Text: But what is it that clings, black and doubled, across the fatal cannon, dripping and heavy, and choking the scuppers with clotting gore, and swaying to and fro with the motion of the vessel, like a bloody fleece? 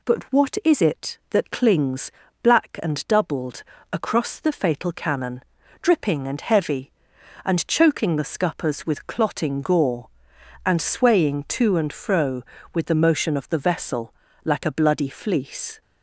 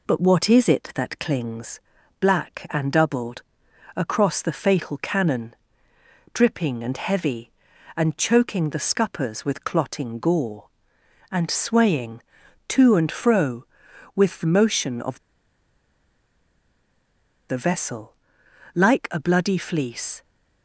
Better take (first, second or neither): first